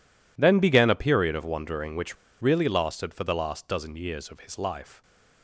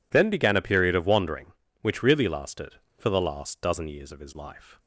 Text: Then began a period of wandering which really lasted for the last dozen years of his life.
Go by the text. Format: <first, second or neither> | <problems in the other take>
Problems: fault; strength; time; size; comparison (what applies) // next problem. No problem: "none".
second | pauses between "which" and "really"; slight; at 2.1 s; 0.26 s long